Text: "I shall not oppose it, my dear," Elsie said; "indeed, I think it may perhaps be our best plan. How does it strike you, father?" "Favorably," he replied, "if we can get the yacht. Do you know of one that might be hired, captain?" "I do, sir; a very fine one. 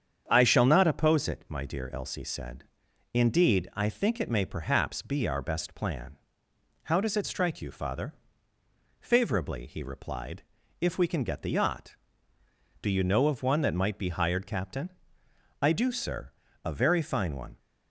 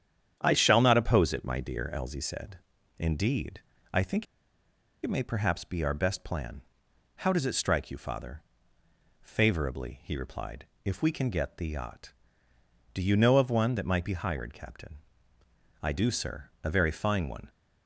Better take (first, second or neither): first